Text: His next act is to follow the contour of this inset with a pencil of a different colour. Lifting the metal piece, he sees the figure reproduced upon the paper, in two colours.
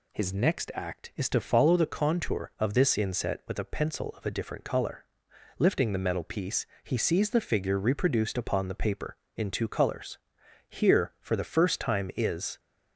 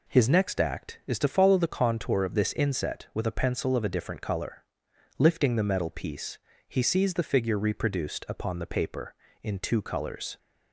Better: second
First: goes on to say "Here for the first time is"; strong; from 10.6 s on; 1.9 s long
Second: none

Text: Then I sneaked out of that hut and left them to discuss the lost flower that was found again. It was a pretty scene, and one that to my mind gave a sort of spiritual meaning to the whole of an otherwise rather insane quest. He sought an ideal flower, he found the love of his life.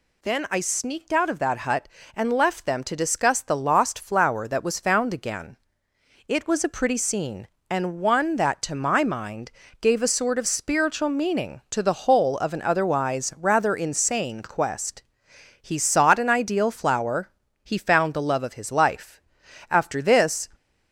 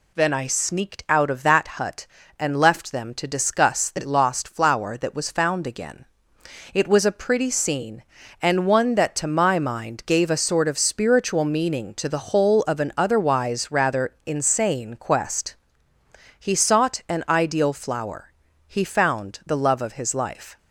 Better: second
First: pauses between "mind" and "gave"; slight; at 9.5 s; 0.30 s long // goes on to say "After this"; noticeable; from 19.7 s on; 0.78 s long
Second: none

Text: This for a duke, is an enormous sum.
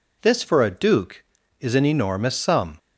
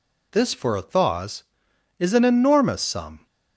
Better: first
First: none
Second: says "thaws" for "duke"; at 0.8 s

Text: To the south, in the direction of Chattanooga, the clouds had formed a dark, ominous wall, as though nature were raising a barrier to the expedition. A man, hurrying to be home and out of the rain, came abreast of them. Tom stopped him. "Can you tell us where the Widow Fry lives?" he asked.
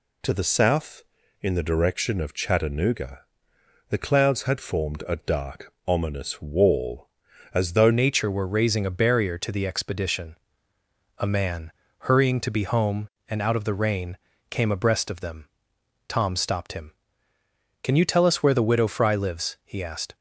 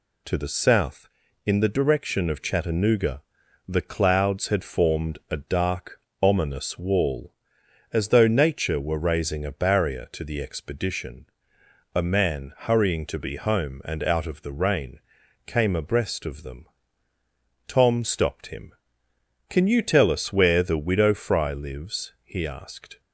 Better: second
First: changes voice at "nature"; from 7.9 s on; 12.2 s long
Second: none

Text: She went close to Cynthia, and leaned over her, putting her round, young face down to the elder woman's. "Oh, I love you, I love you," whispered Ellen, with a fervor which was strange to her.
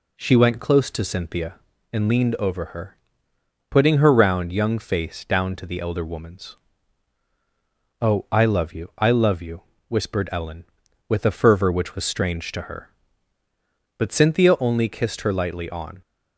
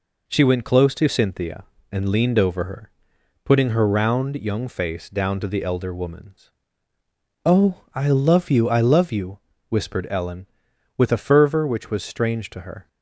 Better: second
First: goes on to say "But Cynthia only kissed her lightly on"; strong; from 13.9 s on; 2.0 s long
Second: none

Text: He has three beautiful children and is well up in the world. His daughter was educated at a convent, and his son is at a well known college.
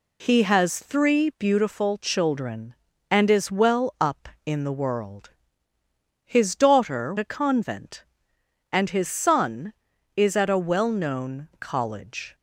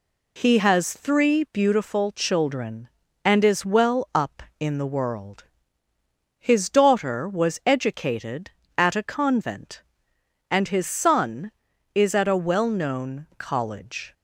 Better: second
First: skips "was educated at"; at 7.1 s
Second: none

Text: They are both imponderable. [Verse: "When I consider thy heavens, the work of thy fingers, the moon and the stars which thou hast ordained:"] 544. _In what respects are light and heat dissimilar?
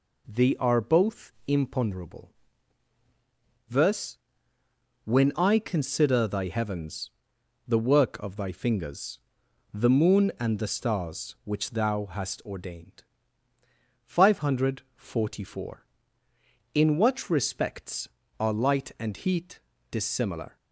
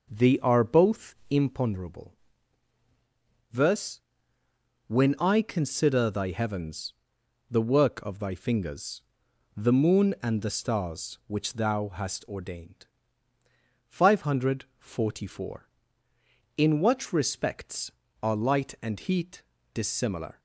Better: first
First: pauses between "heat" and "dissimilar"; slight; at 19.5 s; 0.30 s long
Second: starts louder than the rest; noticeable; until 1.6 s; 5.5 dB // pauses between "heat" and "dissimilar"; slight; at 19.4 s; 0.30 s long

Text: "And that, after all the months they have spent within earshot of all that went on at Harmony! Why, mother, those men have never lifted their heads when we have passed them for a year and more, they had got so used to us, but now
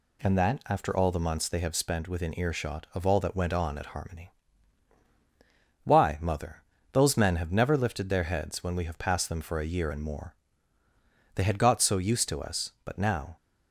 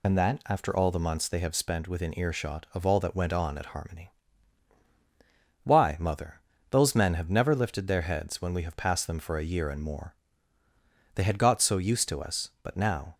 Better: first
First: none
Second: loses the start of "And"; at 0.0 s; 45 ms

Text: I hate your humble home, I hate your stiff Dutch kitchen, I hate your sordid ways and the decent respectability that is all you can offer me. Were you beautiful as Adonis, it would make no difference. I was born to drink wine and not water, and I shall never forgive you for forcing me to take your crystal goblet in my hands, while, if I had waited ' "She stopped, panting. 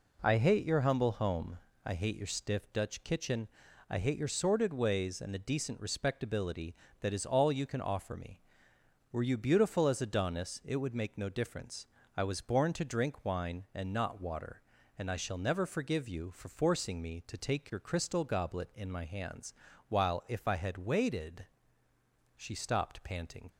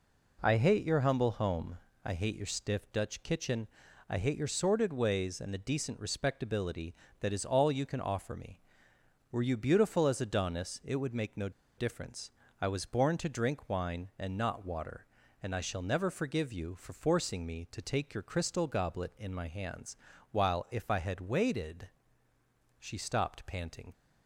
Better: first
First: none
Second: pauses between "no" and "difference"; slight; at 11.4 s; 0.27 s long

